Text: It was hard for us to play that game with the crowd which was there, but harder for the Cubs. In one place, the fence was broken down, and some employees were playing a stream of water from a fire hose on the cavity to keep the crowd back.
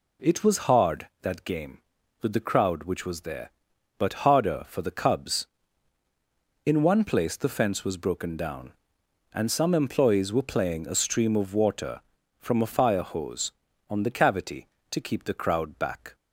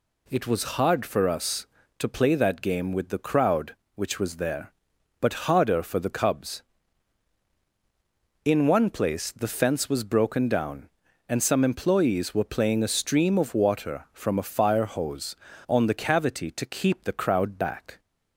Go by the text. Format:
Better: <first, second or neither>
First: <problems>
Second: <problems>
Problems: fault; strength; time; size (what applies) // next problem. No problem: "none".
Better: second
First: skips "for us to play"; at 1.1 s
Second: none